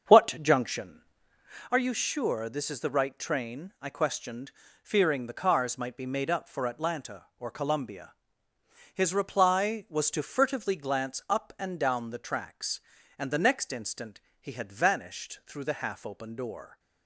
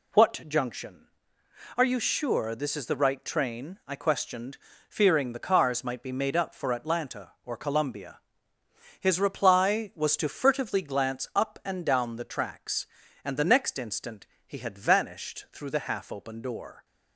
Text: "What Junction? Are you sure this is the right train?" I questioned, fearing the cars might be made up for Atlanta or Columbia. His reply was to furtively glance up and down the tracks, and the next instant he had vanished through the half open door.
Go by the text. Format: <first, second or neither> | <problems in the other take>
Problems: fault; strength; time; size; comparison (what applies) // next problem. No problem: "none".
second | starts louder than the rest; strong; until 1.6 s; 7 dB // pauses between "instant" and "he"; slight; at 14.1 s; 0.22 s long; slight in the second